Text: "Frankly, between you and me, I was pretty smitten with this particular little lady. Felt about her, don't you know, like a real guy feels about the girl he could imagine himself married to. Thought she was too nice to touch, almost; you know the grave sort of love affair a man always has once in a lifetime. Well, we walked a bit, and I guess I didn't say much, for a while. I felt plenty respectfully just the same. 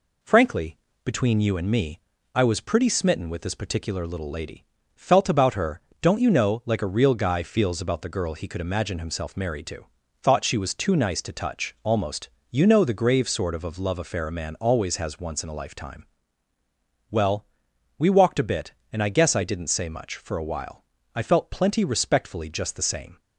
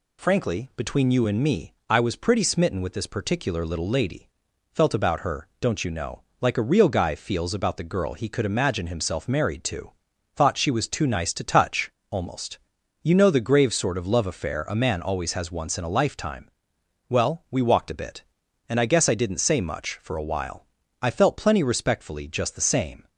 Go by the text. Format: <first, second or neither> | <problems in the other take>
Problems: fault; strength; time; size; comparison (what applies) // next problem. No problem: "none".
second | says "of" twice; at 13.6 s